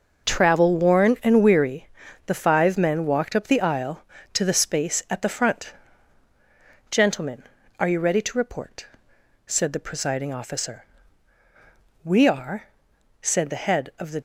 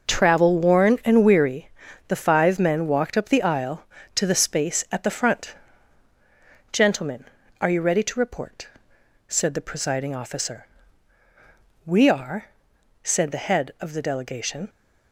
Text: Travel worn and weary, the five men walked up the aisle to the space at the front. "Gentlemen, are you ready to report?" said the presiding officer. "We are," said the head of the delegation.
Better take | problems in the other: second | stops before "delegation"; at 14.1 s

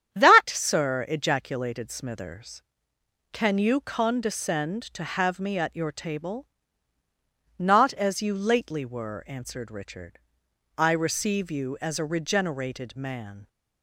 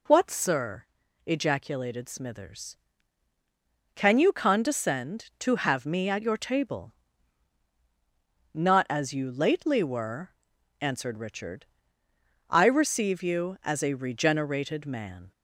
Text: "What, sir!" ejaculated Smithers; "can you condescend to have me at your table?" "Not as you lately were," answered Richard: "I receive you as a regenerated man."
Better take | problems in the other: second | starts louder than the rest; strong; until 1.1 s; 9.5 dB // says "That" for "What"; at 0.1 s

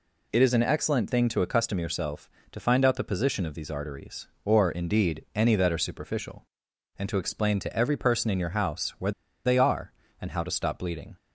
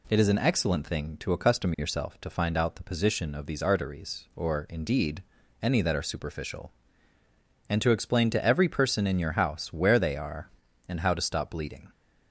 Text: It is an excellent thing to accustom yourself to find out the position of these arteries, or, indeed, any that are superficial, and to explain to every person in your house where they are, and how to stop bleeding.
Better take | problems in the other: second | pauses between "where" and "they"; slight; at 9.1 s; 0.33 s long

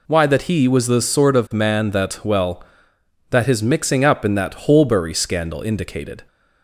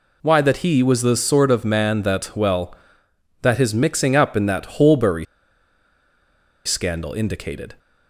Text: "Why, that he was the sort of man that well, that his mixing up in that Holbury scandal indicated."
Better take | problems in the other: first | pauses between "Holbury" and "scandal"; strong; at 5.2 s; 1.4 s long

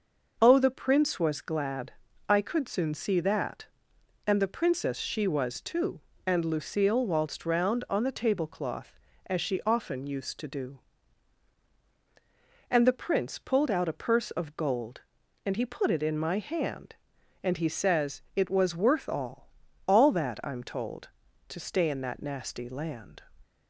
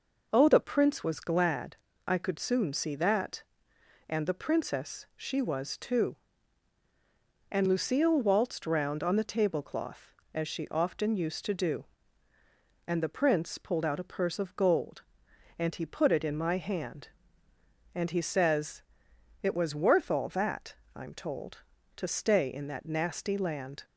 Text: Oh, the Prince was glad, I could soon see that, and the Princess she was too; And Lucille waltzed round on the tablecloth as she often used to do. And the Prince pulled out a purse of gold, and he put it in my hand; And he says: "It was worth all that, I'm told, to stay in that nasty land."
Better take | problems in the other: second | says "all" twice; at 19.8 s

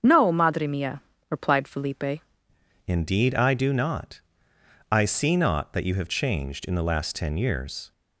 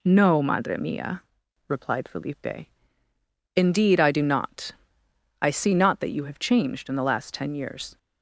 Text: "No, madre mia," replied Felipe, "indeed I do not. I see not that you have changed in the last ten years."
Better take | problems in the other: second | starts louder than the rest; strong; until 1.0 s; 7 dB // changes voice at "indeed"; from 2.8 s on; 5.1 s long

